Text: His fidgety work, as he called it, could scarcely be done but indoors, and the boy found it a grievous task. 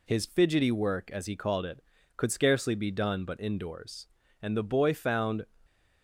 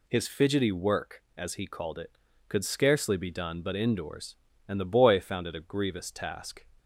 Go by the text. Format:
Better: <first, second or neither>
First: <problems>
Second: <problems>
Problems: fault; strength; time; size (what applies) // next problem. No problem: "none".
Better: second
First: stops before "it a grievous task"; at 5.6 s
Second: none